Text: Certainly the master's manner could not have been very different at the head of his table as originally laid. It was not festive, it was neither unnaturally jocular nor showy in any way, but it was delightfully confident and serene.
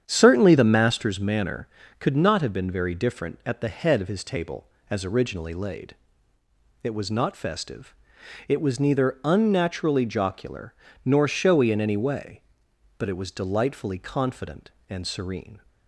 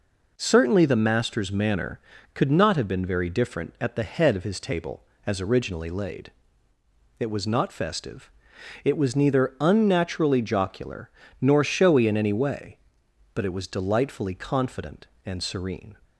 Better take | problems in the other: second | starts louder than the rest; strong; until 1.3 s; 8.5 dB // pauses between "jocular" and "nor"; slight; at 10.7 s; 0.30 s long; slight in the second

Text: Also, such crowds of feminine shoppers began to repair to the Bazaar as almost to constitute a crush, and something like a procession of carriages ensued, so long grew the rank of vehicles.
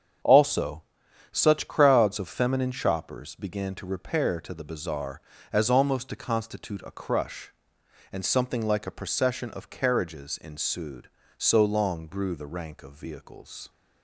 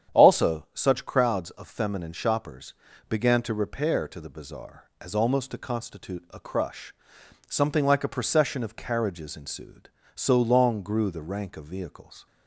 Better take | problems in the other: first | starts louder than the rest; strong; until 1.2 s; 9 dB; strong in the first // pauses between "shoppers" and "began"; slight; at 2.7 s; 0.36 s long // skips "and"; at 7.2 s

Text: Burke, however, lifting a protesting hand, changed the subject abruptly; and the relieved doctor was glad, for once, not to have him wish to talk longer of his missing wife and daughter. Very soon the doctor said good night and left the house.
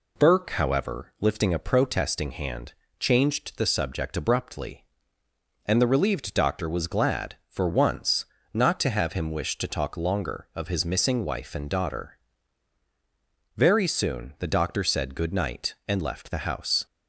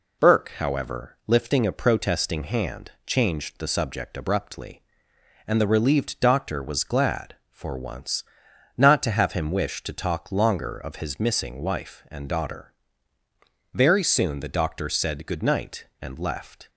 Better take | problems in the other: first | stops before "the house"; at 16.6 s

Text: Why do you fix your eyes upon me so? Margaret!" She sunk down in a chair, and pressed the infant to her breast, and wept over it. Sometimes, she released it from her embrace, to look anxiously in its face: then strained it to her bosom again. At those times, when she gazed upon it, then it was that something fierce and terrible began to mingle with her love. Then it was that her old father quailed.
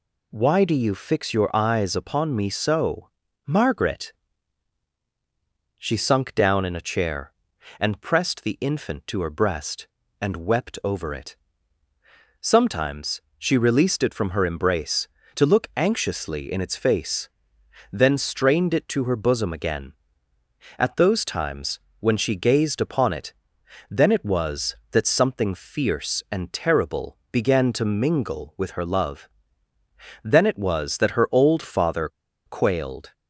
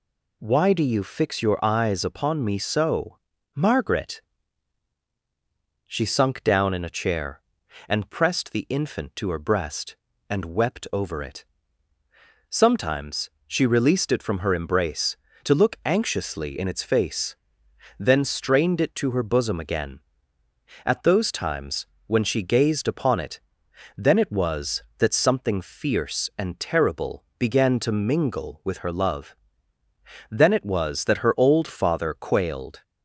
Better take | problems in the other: second | pauses between "terrible" and "began"; slight; at 27.1 s; 0.16 s long; slight in the second // pauses between "father" and "quailed"; at 32.0 s; 0.38 s long

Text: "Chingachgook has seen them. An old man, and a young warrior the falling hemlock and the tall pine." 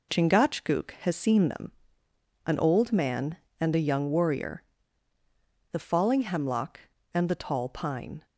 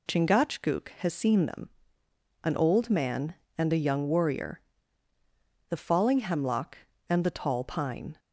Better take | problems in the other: second | gets quieter; noticeable; throughout; 5.5 dB // pauses between "warrior" and "the"; at 4.6 s; 1.1 s long; also in the second

